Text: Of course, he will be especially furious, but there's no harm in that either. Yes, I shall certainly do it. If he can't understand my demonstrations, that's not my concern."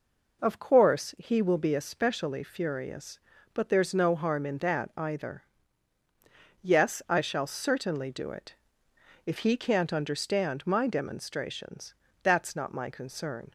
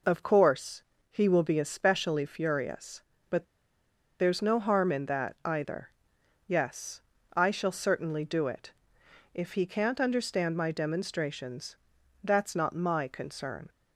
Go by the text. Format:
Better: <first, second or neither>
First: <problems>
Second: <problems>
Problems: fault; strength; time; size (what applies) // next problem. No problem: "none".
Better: first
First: none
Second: pauses between "but" and "there's"; noticeable; at 3.4 s; 0.75 s long